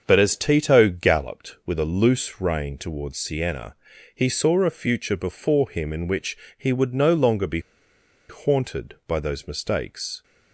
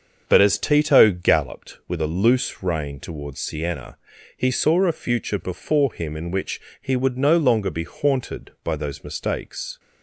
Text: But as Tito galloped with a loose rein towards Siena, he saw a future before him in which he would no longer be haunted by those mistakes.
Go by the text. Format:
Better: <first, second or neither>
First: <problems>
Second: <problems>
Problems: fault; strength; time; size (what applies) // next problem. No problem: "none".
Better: second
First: starts louder than the rest; until 1.0 s; 6.5 dB // pauses between "which" and "he"; slight; at 6.3 s; 0.22 s long // pauses between "be" and "haunted"; noticeable; at 7.5 s; 0.69 s long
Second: starts louder than the rest; until 1.2 s; 6.5 dB // pauses between "which" and "he"; slight; at 6.5 s; 0.22 s long